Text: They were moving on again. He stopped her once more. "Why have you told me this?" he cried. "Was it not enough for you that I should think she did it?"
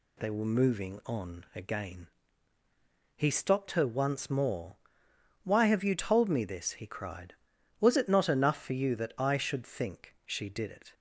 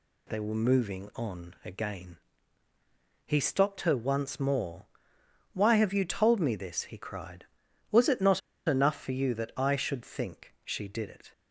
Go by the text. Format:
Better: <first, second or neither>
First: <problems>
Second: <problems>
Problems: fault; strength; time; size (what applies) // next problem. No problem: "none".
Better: first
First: none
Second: pauses between "not" and "enough"; slight; at 8.4 s; 0.27 s long